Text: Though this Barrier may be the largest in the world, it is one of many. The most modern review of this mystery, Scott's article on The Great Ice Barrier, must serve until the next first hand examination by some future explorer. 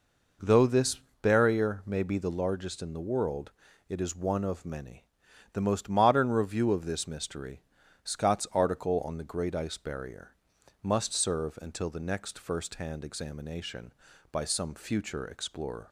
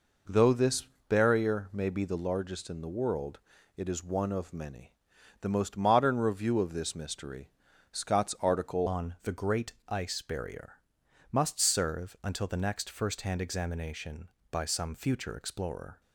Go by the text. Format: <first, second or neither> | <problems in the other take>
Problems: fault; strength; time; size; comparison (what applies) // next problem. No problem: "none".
first | pauses between "this" and "Barrier"; slight; at 0.8 s; 0.22 s long; slight in the first // changes voice at "on"; from 8.8 s on; 7.2 s long // pauses between "Great" and "Ice"; slight; at 9.7 s; 0.16 s long